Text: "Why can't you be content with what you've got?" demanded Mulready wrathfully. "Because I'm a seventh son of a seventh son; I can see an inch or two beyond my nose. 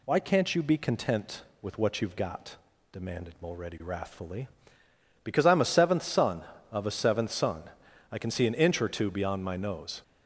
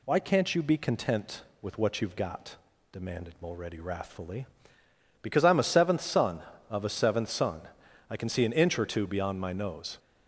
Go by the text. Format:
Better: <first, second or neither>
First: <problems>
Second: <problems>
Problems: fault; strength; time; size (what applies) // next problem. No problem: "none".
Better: neither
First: none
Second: none